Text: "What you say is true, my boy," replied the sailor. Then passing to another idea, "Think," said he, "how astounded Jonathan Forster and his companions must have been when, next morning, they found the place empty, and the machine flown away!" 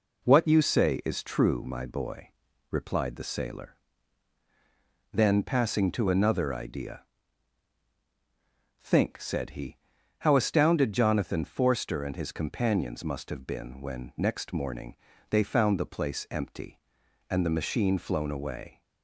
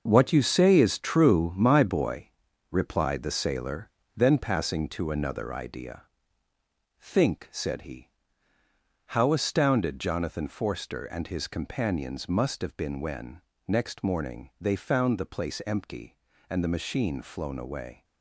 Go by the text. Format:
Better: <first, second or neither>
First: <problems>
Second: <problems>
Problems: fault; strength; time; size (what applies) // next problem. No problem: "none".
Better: first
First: none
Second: gets quieter; strong; throughout; 9.5 dB